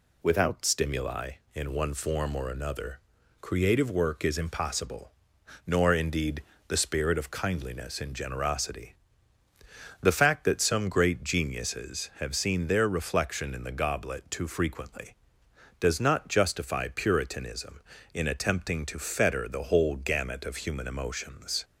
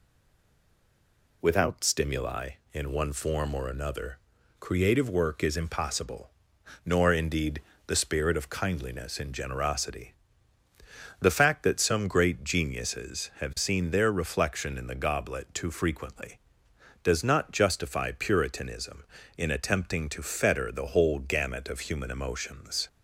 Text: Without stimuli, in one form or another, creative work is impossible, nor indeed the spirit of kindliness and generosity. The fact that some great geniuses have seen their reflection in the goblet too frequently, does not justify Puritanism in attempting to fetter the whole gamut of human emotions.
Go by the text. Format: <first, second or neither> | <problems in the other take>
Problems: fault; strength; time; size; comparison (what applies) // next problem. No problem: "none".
first | stays silent before the first word; noticeable; until 1.4 s; 1.4 s long // pauses between "indeed" and "the"; slight; at 7.6 s; 0.24 s long; slight in the first